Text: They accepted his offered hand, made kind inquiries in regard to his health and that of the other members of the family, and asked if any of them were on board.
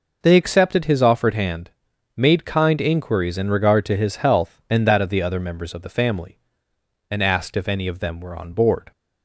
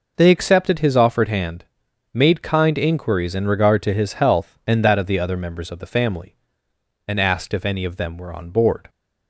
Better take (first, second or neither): neither